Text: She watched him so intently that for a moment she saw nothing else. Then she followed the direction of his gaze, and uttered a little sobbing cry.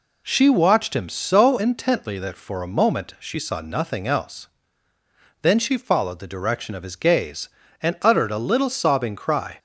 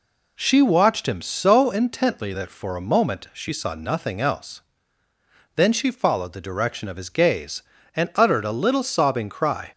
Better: neither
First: none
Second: none

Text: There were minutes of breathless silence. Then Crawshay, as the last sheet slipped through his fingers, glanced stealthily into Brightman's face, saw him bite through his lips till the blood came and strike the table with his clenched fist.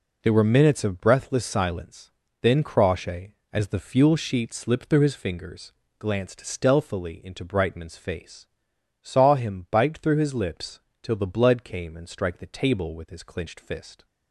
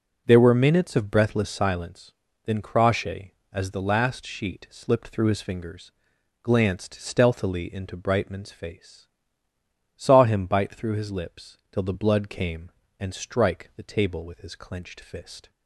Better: second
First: says "fuel" for "last"; at 3.7 s // pauses between "lips" and "till"; slight; at 10.7 s; 0.22 s long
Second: none

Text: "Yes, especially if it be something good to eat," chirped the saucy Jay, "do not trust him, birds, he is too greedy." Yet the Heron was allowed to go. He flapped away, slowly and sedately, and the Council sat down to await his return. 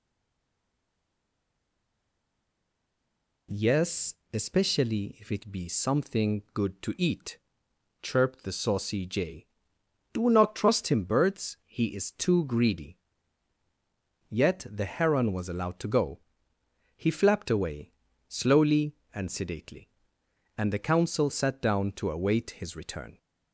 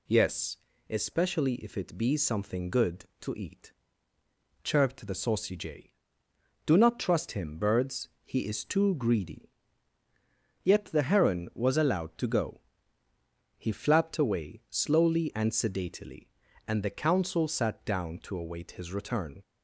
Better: second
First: stays silent before the first word; strong; until 3.4 s; 3.4 s long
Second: none

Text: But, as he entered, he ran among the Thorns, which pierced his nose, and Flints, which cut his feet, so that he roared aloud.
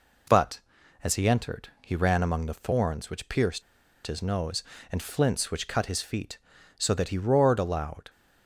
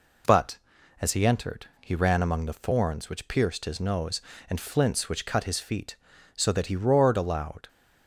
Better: second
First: pauses between "pierced" and "his"; at 3.6 s; 0.43 s long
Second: none

